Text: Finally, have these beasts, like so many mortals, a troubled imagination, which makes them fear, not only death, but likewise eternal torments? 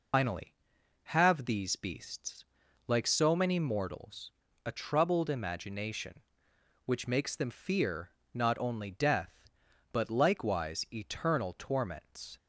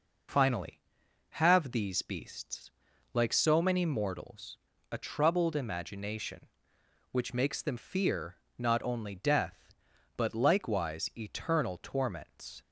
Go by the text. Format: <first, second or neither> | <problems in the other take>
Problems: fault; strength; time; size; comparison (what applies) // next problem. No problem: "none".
second | loses the start of "Finally"; at 0.1 s; 110 ms